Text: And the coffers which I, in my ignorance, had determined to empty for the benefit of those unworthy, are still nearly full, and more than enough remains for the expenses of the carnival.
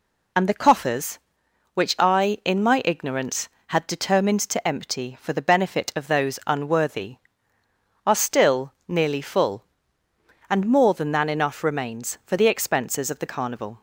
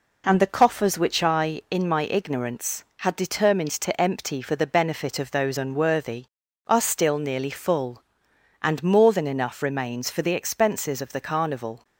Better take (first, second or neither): second